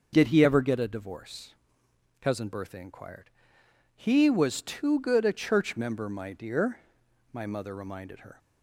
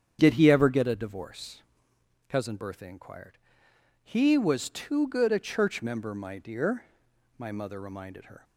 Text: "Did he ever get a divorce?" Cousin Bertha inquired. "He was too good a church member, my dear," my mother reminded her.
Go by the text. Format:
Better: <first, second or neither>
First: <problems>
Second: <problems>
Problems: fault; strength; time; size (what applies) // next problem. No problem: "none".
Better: first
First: none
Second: starts louder than the rest; strong; until 1.9 s; 8.5 dB